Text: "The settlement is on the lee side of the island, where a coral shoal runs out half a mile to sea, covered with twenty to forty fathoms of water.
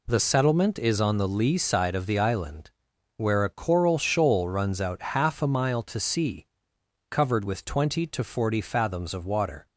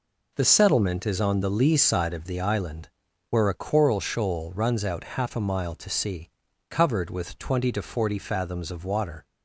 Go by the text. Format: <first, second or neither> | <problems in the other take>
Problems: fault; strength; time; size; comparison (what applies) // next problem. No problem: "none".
neither | none